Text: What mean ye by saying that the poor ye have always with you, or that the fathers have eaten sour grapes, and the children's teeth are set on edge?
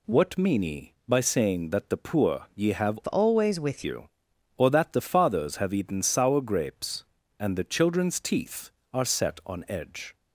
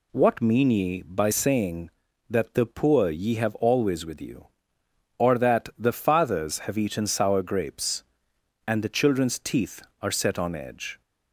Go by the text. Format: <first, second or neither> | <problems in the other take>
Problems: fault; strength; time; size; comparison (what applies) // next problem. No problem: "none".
second | changes voice from "always" to "with"; from 3.0 to 3.8 s; 0.8 s long